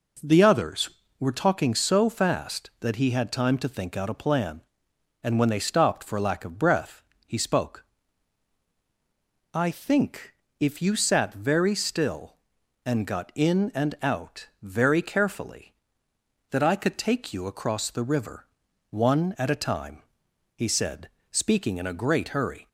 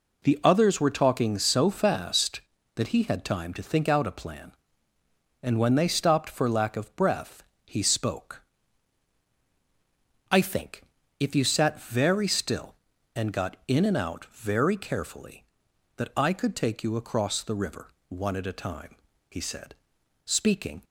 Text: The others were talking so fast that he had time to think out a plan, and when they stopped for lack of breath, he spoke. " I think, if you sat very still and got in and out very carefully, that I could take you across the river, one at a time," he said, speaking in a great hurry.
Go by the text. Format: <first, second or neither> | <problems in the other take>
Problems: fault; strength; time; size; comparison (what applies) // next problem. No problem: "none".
first | stops before "in a great hurry"; at 20.8 s